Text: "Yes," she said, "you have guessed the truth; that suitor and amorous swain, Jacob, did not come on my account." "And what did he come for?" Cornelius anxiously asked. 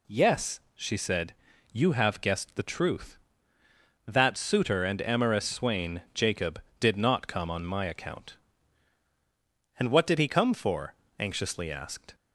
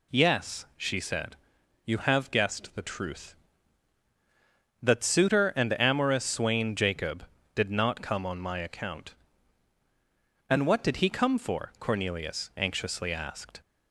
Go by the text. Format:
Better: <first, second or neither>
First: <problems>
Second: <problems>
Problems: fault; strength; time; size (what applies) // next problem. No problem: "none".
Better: second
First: skips "Cornelius"; at 11.0 s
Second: none